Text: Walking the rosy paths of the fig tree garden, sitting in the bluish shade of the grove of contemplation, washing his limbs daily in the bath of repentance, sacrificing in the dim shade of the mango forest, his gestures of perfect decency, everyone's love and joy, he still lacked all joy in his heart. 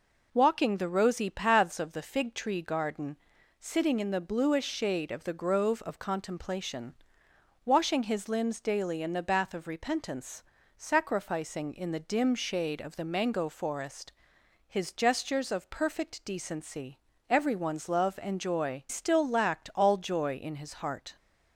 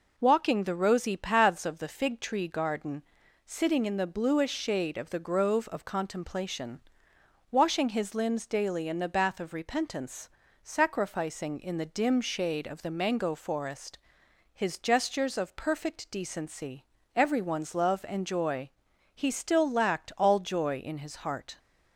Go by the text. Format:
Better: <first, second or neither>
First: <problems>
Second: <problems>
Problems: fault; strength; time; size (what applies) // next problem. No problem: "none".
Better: second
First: skips "he"; at 18.8 s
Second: none